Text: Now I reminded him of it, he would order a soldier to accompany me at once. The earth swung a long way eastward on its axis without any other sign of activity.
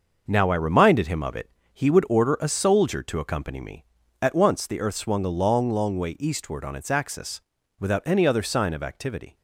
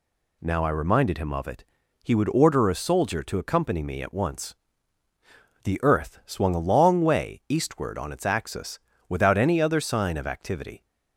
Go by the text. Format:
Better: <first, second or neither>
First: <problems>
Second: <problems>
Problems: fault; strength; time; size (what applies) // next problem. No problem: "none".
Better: second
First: starts louder than the rest; noticeable; until 1.2 s; 6 dB // says "long" twice; at 5.6 s // pauses between "axis" and "without"; at 7.3 s; 0.40 s long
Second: pauses between "axis" and "without"; slight; at 8.7 s; 0.30 s long